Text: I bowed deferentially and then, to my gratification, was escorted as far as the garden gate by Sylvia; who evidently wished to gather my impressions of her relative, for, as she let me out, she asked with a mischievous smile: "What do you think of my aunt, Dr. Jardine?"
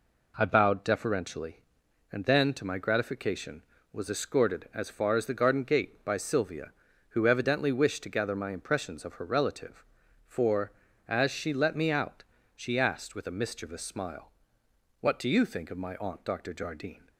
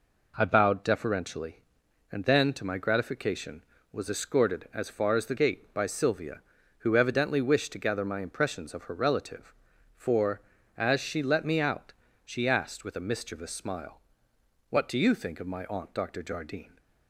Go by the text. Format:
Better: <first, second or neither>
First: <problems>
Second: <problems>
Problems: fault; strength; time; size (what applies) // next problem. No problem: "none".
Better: first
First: none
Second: skips "garden"; at 5.3 s